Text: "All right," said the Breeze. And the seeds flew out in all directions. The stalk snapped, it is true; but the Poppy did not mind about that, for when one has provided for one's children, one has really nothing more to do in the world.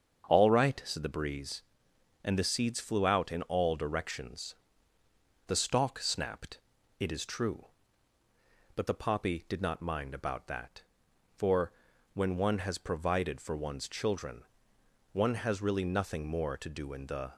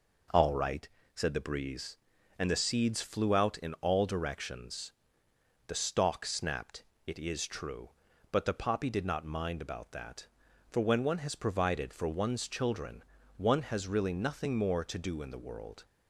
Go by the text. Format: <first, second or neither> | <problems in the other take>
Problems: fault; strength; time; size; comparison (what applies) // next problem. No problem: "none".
second | starts louder than the rest; strong; until 1.2 s; 7 dB // pauses between "for" and "when"; at 11.7 s; 0.44 s long // stops before "world"; at 17.3 s